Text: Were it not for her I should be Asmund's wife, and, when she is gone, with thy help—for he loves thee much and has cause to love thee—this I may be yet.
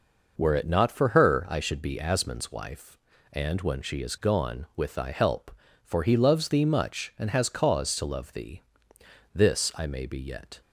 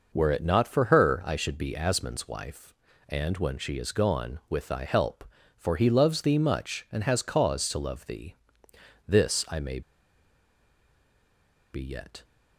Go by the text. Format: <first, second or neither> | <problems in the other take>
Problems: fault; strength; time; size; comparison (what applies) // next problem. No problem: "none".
first | pauses between "may" and "be"; strong; at 9.7 s; 1.9 s long